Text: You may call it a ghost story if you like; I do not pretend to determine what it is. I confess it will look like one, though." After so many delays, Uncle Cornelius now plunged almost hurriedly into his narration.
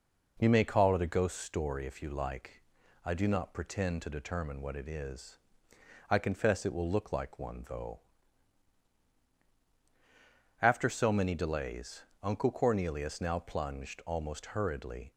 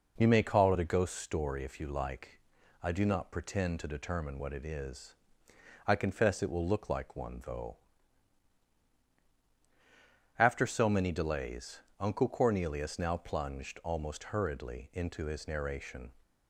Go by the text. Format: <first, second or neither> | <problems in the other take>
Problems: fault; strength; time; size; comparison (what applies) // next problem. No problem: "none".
second | stops before "into his narration"; at 15.1 s